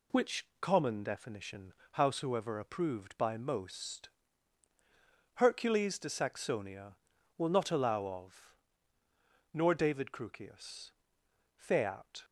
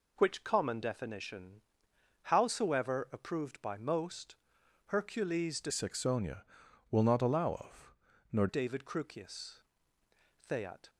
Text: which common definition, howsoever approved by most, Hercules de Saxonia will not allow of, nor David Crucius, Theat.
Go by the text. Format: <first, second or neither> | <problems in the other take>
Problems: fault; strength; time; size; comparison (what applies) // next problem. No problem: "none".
first | changes voice from "Saxonia" to "nor"; from 5.6 to 8.4 s; 2.8 s long